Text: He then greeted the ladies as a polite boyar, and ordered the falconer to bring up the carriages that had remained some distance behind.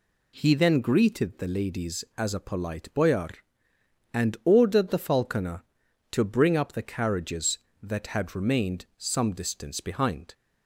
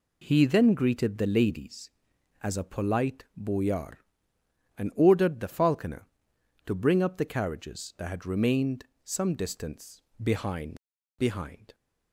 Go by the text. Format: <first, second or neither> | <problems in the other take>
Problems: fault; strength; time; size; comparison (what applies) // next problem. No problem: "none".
first | pauses between "remained" and "some"; slight; at 8.8 s; 0.18 s long // pauses between "distance" and "behind"; slight; at 10.0 s; 0.22 s long // says "behind" twice; at 11.1 s